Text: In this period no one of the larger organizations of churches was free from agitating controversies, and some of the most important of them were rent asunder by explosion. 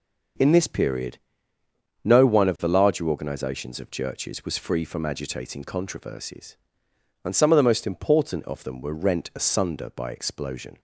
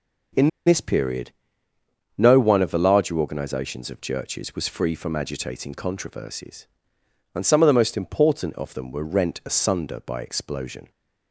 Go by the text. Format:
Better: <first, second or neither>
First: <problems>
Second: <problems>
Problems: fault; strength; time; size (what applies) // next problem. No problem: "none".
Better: first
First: pauses between "period" and "no"; noticeable; at 1.1 s; 0.88 s long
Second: pauses between "In" and "this"; slight; at 0.4 s; 0.18 s long // pauses between "period" and "no"; noticeable; at 1.3 s; 0.88 s long